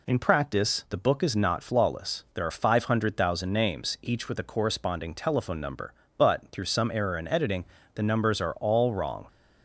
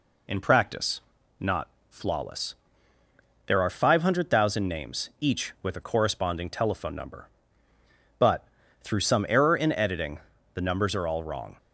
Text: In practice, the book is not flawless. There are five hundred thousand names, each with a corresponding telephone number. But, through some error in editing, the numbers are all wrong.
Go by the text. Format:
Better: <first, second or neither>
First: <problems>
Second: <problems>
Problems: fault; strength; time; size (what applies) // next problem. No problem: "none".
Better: first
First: none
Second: skips "the book is"; at 1.2 s // pauses between "not" and "flawless"; slight; at 1.6 s; 0.22 s long